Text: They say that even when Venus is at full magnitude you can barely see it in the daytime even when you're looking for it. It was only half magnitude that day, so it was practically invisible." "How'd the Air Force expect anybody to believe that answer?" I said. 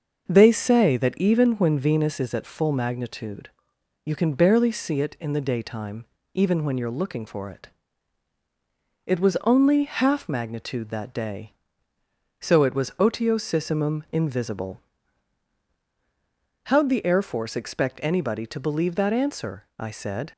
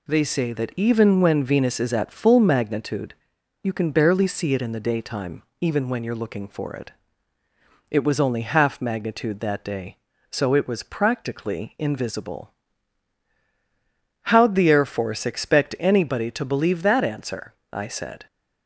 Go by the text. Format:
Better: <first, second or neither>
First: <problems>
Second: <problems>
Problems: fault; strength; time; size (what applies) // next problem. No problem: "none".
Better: second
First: starts louder than the rest; until 1.3 s; 6 dB // pauses between "magnitude" and "you"; noticeable; at 3.4 s; 0.54 s long // pauses between "daytime" and "even"; slight; at 6.0 s; 0.30 s long // says "otiosissimum" for "practically"; at 12.9 s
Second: pauses between "magnitude" and "you"; noticeable; at 3.1 s; 0.48 s long // pauses between "daytime" and "even"; slight; at 5.4 s; 0.18 s long